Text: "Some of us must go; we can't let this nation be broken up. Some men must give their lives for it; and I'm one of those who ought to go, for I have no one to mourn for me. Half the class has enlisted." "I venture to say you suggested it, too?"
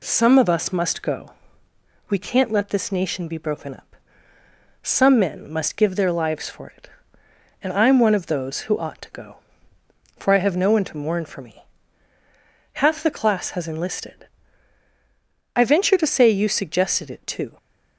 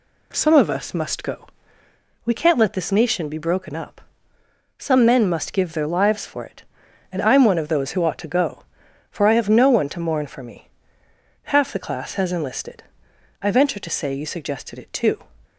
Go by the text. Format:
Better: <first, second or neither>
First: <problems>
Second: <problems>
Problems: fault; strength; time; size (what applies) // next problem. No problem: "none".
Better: neither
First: none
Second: none